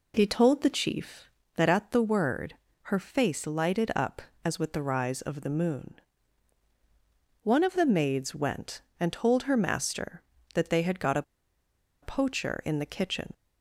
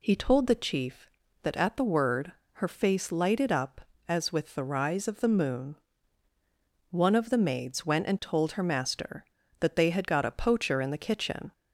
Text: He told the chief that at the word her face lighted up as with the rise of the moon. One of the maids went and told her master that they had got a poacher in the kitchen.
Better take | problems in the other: second | pauses between "word" and "her"; slight; at 2.5 s; 0.28 s long; slight in the second // pauses between "a" and "poacher"; noticeable; at 11.2 s; 0.79 s long

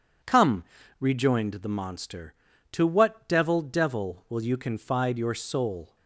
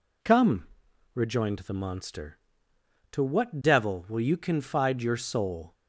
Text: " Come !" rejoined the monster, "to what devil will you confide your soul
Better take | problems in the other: second | starts louder than the rest; until 1.4 s; 6.5 dB // says "devil" twice; at 3.6 s

